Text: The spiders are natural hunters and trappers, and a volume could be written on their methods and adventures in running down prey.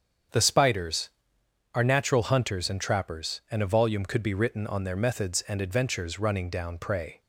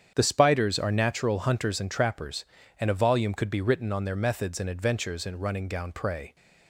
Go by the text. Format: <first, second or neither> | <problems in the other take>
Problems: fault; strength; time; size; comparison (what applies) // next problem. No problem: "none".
second | starts louder than the rest; strong; until 1.9 s; 7.5 dB; strong in the second // skips "in"; at 6.1 s